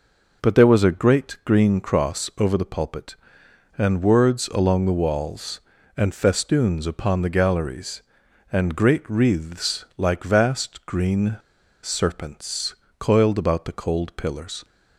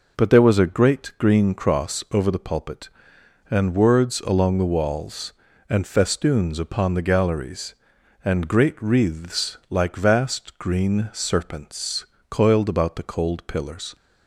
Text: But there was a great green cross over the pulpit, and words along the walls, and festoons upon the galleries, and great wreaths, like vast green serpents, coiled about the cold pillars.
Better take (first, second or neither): second